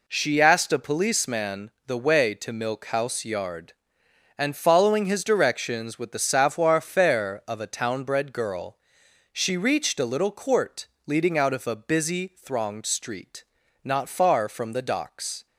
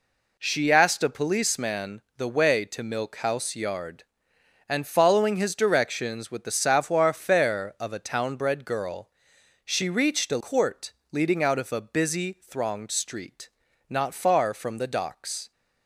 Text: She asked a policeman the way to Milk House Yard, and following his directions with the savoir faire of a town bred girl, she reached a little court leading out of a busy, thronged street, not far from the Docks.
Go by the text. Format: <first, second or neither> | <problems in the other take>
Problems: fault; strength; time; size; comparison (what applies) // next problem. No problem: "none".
first | pauses between "policeman" and "the"; slight; at 2.0 s; 0.16 s long; slight in the first // skips "little"; at 10.3 s // pauses between "court" and "leading"; slight; at 10.9 s; 0.22 s long; slight in the first